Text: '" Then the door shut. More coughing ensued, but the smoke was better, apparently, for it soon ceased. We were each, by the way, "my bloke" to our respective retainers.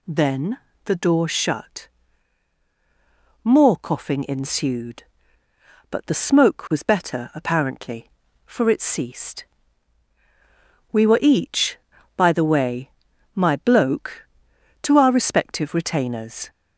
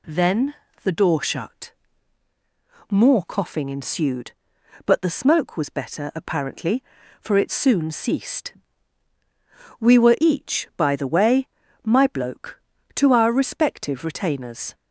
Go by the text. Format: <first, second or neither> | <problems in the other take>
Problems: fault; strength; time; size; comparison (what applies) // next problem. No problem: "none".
second | pauses between "Then" and "the"; slight; at 0.5 s; 0.28 s long; slight in the second // skips "soon"; at 8.8 s